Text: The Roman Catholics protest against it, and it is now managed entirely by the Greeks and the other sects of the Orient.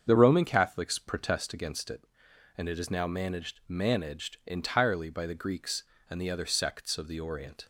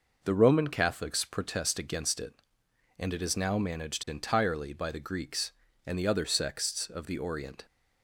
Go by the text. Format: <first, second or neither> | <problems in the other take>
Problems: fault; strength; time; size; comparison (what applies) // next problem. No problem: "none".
second | starts louder than the rest; strong; until 1.0 s; 7 dB // says "managed" twice; at 3.6 s